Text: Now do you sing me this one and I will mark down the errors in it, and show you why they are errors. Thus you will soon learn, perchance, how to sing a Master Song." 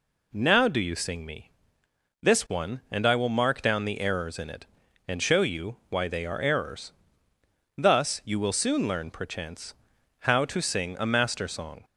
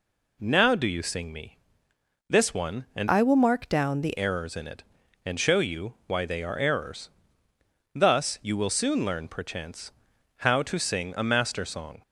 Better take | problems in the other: first | pauses between "me" and "this"; noticeable; at 1.5 s; 0.72 s long; noticeable in the first // changes voice from "I" to "the"; from 3.0 to 4.1 s; 1.1 s long

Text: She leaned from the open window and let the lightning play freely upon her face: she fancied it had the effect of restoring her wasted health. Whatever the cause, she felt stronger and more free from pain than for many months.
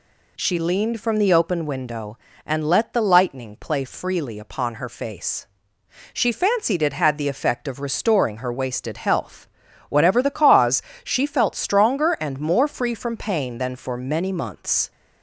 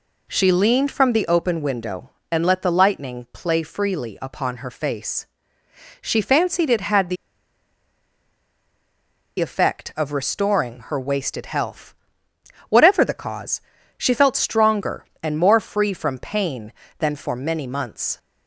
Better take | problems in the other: first | pauses between "the" and "effect"; strong; at 7.1 s; 2.2 s long

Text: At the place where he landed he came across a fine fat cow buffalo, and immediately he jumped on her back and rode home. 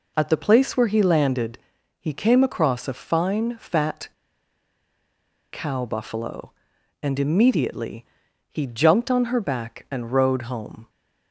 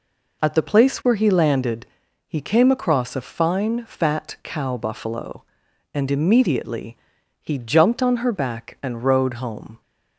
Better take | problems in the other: second | pauses between "landed" and "he"; at 1.5 s; 0.42 s long; also in the second // pauses between "fat" and "cow"; strong; at 4.0 s; 1.4 s long // pauses between "immediately" and "he"; noticeable; at 8.0 s; 0.46 s long; noticeable in the second

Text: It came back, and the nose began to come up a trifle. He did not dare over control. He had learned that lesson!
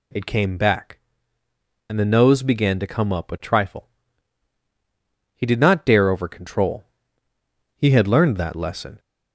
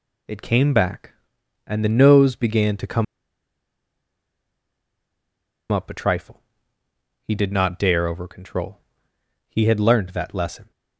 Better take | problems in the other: first | pauses between "come" and "up"; strong; at 3.0 s; 2.6 s long

